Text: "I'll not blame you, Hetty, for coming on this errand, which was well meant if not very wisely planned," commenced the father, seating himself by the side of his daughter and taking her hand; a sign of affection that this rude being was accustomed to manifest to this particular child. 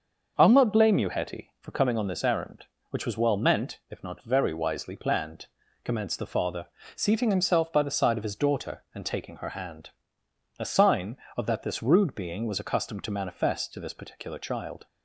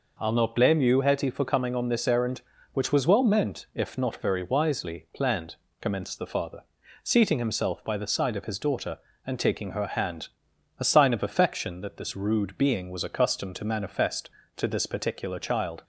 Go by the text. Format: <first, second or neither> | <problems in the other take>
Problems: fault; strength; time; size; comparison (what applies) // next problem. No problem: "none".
second | starts louder than the rest; until 1.3 s; 6.5 dB // skips "affection"; at 11.4 s